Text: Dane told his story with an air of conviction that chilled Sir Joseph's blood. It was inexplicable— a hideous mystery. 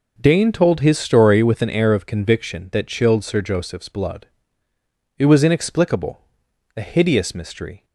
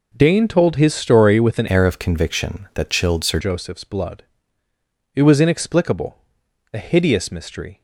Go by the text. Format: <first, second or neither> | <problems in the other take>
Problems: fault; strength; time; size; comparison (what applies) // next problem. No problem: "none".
first | changes voice from "air" to "Sir"; from 1.7 to 3.3 s; 1.6 s long